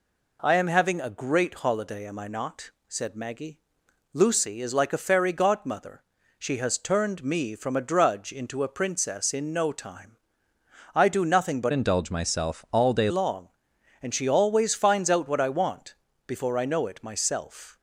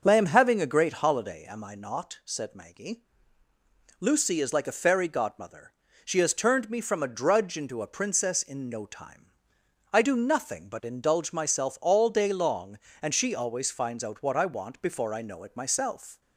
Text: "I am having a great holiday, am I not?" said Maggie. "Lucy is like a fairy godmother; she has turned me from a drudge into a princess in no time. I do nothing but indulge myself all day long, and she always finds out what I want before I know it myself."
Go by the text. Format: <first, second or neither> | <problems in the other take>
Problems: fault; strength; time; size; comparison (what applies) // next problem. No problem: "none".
second | changes voice from "indulge" to "day"; from 11.7 to 13.0 s; 1.3 s long // pauses between "want" and "before"; slight; at 15.9 s; 0.34 s long